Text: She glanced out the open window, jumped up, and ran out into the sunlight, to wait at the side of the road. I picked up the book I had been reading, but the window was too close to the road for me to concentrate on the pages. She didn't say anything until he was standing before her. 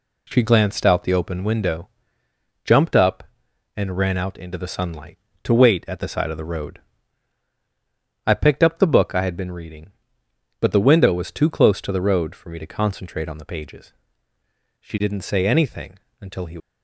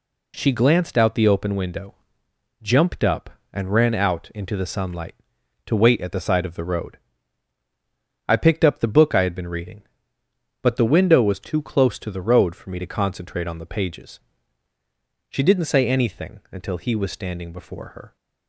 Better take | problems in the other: second | pauses between "anything" and "until"; slight; at 15.9 s; 0.22 s long // stops before "was standing before her"; at 16.5 s

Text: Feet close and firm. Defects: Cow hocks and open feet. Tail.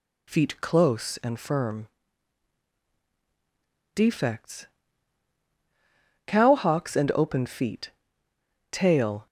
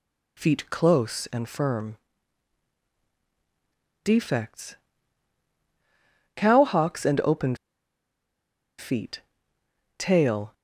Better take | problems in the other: first | pauses between "open" and "feet"; at 7.5 s; 1.2 s long

